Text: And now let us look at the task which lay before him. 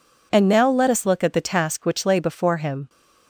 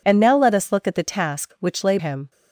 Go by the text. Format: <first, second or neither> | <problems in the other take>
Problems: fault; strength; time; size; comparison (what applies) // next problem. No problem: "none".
first | skips "before"; at 1.9 s